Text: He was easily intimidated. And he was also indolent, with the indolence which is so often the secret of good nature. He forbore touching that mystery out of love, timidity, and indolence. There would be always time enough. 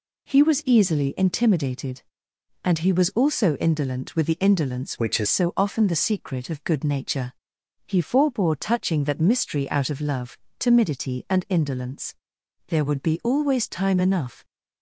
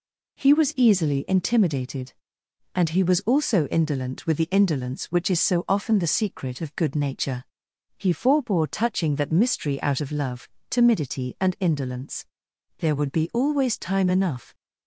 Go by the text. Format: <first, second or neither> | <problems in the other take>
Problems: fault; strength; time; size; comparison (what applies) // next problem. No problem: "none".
second | changes voice from "which" to "is"; from 4.9 to 5.2 s; 0.3 s long